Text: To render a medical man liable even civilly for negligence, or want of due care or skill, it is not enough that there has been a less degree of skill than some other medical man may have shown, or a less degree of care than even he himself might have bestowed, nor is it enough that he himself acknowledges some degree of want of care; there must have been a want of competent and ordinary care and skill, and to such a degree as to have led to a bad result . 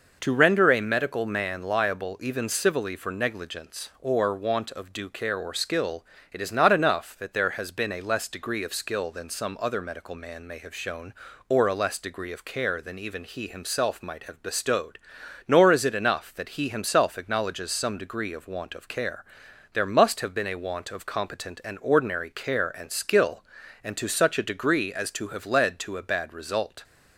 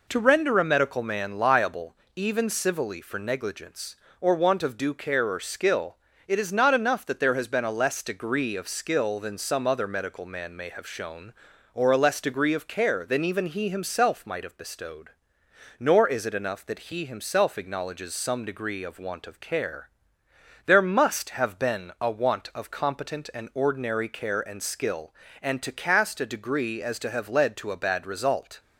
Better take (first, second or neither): first